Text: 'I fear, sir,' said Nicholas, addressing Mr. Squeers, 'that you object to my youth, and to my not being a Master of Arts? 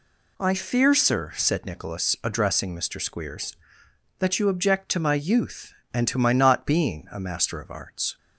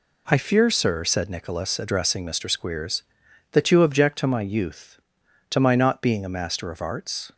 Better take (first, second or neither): first